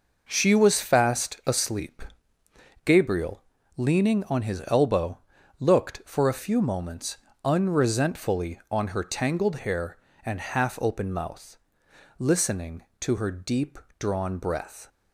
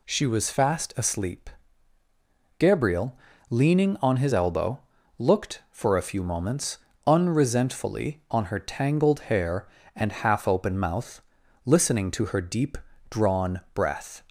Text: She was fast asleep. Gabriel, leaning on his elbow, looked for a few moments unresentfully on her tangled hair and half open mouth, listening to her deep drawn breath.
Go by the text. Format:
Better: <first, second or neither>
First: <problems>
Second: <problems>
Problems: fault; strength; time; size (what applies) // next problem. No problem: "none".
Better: neither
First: pauses between "moments" and "unresentfully"; slight; at 7.1 s; 0.26 s long // pauses between "deep" and "drawn"; slight; at 13.7 s; 0.22 s long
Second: pauses between "moments" and "unresentfully"; slight; at 6.7 s; 0.28 s long // pauses between "deep" and "drawn"; slight; at 12.7 s; 0.32 s long